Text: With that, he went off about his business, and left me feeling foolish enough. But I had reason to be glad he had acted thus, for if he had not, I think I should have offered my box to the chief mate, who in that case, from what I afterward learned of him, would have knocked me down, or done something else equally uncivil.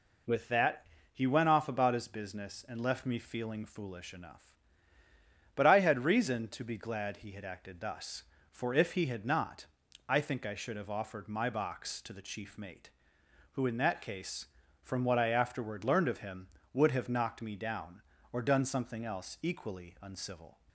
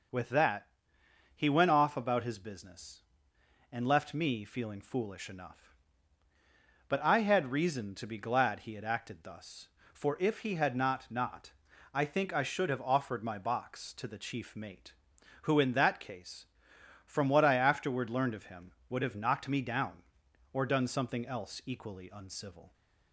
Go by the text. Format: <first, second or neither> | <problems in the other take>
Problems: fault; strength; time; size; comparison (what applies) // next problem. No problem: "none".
first | says "not" twice; at 11.1 s